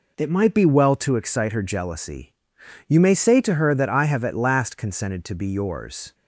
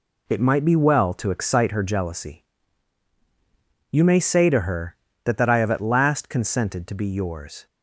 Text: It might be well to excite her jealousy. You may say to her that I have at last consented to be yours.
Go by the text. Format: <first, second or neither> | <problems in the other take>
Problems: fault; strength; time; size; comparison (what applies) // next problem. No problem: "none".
first | says "that" twice; at 5.3 s